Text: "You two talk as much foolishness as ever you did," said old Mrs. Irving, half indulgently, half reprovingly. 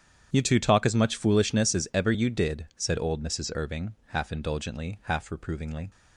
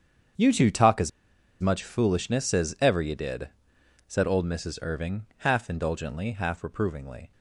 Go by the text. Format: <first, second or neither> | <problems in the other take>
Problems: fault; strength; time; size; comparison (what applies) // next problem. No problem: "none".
first | starts louder than the rest; strong; until 1.9 s; 7.5 dB; strong in the first // pauses between "as" and "much"; noticeable; at 1.1 s; 0.53 s long